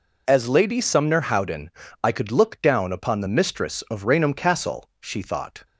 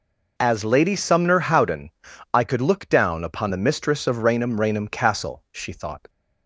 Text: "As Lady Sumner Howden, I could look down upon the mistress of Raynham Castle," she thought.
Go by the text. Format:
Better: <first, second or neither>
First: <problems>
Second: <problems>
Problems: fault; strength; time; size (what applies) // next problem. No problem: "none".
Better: first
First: none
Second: says "Raynham" twice; at 4.5 s